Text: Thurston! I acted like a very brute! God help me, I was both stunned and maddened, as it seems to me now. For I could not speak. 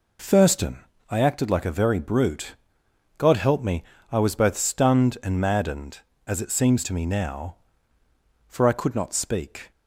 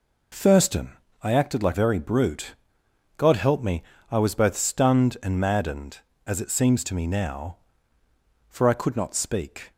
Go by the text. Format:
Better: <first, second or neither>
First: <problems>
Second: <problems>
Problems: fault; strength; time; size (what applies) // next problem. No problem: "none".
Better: first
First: none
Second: skips "a"; at 1.7 s